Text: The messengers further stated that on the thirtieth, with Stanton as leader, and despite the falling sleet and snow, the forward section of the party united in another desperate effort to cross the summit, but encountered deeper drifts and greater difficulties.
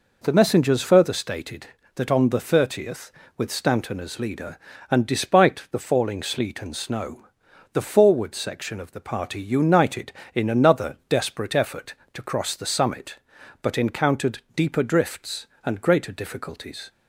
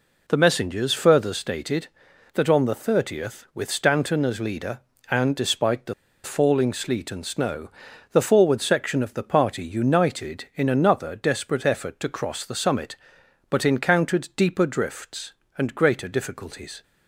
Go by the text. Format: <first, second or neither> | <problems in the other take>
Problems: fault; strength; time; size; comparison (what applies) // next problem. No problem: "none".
first | pauses between "the" and "falling"; slight; at 5.9 s; 0.30 s long